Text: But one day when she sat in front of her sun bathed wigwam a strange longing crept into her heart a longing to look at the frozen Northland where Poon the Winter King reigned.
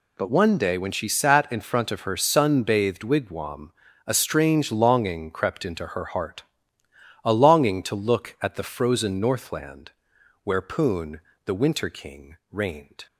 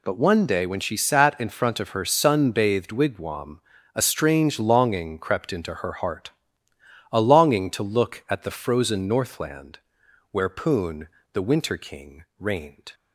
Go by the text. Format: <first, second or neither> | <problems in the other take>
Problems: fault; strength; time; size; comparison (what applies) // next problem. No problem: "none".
neither | pauses between "wigwam" and "a"; slight; the same in both // pauses between "heart" and "a"; noticeable; the same in both // pauses between "Northland" and "where"; noticeable; the same in both // pauses between "Poon" and "the"; slight; the same in both // pauses between "King" and "reigned"; slight; the same in both